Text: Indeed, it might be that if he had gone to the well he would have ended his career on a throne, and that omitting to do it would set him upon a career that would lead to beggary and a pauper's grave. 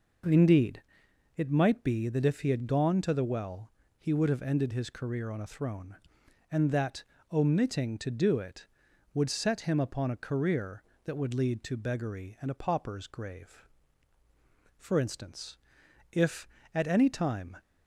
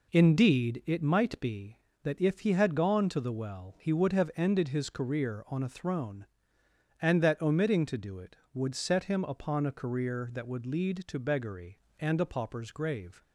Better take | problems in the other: second | pauses between "well" and "he"; slight; at 3.7 s; 0.28 s long // pauses between "that" and "omitting"; slight; at 7.0 s; 0.28 s long // goes on to say "For instance if at any time"; strong; from 14.7 s on; 2.8 s long

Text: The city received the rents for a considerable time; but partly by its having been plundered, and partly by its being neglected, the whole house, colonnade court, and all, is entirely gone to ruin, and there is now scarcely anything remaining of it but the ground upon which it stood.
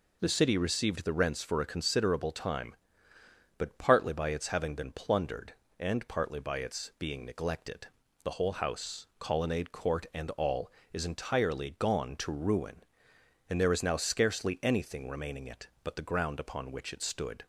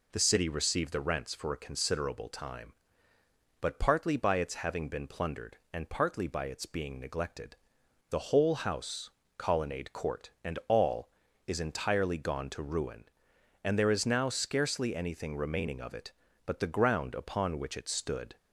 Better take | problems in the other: second | skips "of"; at 15.4 s

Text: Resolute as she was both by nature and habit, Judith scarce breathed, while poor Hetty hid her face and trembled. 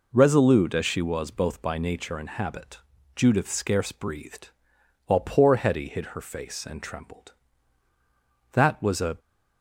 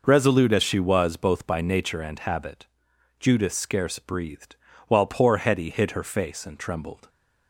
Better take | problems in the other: second | goes on to say "That was a"; noticeable; from 8.5 s on; 0.66 s long

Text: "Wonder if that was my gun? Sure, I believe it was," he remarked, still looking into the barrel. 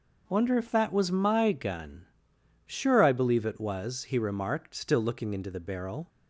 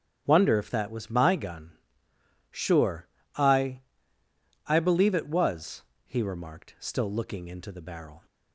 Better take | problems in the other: first | starts louder than the rest; strong; until 1.2 s; 9 dB // says "I" twice; at 4.6 s

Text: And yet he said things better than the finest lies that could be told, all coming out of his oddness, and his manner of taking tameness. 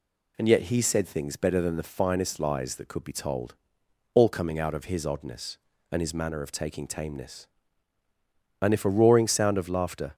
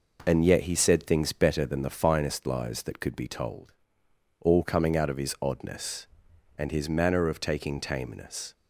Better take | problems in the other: second | goes on to say "And if a roaring sound of laughter"; from 8.6 s on; 1.5 s long

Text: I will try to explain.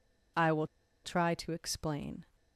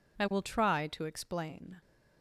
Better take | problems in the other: second | pauses between "will" and "try"; at 0.6 s; 0.36 s long

